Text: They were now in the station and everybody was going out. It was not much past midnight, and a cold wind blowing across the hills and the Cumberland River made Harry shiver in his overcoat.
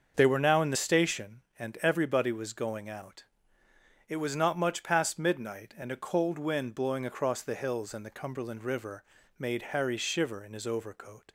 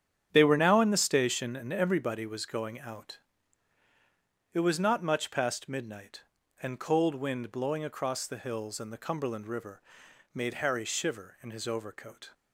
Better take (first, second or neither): first